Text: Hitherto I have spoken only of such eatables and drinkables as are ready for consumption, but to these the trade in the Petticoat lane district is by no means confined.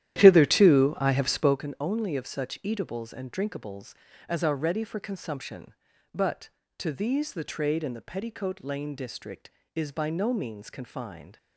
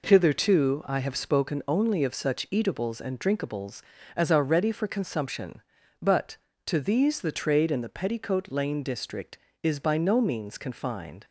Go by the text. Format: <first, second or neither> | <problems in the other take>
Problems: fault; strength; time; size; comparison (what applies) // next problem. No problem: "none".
second | starts louder than the rest; strong; until 1.7 s; 12 dB